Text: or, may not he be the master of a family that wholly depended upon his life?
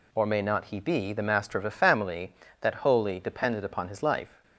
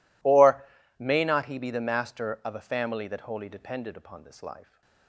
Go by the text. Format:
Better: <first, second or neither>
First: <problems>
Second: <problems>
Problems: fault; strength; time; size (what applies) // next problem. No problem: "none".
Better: first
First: none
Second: says "this" for "his"; at 4.2 s